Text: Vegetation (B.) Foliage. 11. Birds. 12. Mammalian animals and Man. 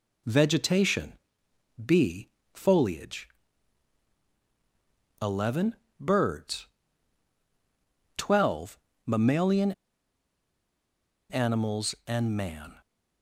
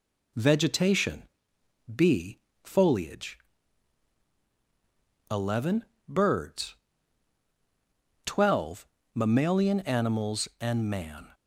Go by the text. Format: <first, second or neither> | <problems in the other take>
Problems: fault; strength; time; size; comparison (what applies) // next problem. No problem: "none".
second | pauses between "Mammalian" and "animals"; strong; at 9.7 s; 1.5 s long